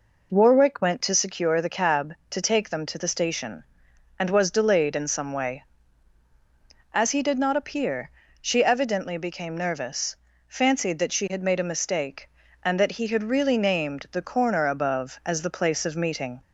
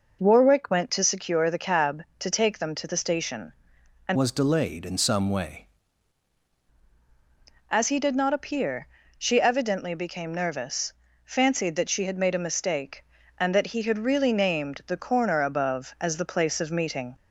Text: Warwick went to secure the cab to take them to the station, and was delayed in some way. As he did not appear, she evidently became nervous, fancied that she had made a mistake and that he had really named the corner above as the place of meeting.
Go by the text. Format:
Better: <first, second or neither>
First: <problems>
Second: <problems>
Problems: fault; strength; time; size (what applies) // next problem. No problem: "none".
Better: first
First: none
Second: changes voice from "was" to "way"; from 4.1 to 5.6 s; 1.5 s long